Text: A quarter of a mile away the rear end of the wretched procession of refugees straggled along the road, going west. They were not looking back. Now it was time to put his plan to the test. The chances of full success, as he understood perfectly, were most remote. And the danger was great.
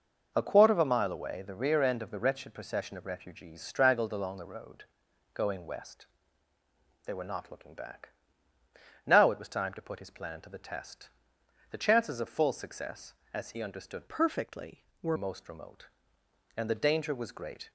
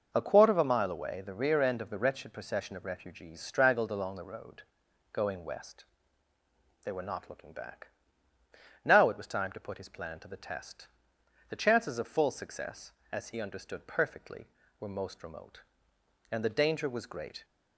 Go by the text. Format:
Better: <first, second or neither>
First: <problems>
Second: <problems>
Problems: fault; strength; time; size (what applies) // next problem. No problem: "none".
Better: second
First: changes voice from "perfectly" to "were"; from 14.0 to 15.1 s; 1.1 s long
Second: none